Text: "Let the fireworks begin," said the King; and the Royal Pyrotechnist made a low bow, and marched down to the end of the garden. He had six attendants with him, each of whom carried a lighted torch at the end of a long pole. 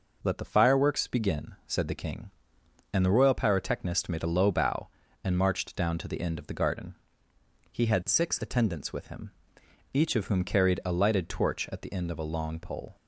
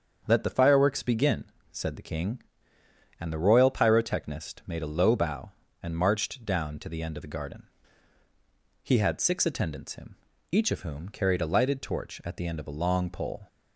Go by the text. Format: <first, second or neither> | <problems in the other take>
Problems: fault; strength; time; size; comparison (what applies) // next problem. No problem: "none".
first | starts louder than the rest; until 1.2 s; 7 dB // skips "with"; at 9.9 s